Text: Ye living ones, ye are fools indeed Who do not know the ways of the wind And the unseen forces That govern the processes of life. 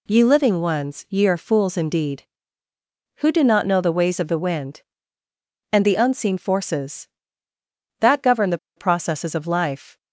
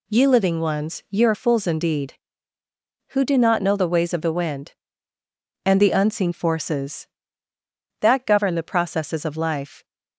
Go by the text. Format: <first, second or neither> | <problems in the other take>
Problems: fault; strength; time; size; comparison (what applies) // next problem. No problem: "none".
second | pauses between "the" and "processes"; slight; at 8.5 s; 0.18 s long